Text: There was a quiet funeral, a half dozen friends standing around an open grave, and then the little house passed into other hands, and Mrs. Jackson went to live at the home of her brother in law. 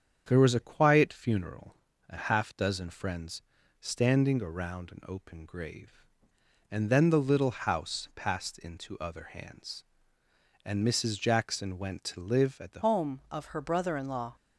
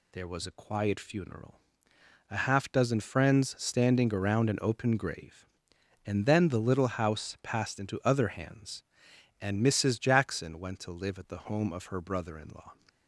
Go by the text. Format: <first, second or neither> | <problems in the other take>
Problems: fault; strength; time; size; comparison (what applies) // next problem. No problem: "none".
second | starts louder than the rest; strong; until 1.2 s; 7.5 dB // pauses between "friends" and "standing"; at 3.4 s; 0.38 s long // changes voice at "home"; from 12.8 s on; 1.5 s long